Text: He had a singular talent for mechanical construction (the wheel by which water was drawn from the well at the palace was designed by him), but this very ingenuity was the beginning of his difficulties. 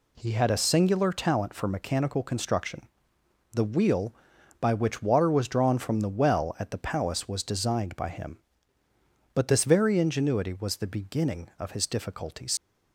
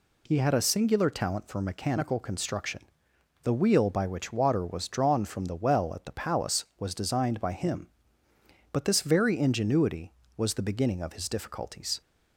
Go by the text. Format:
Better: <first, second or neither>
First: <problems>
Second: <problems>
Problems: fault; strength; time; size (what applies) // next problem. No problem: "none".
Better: second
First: leaves "difficulties" unfinished; at 12.5 s; 70 ms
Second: none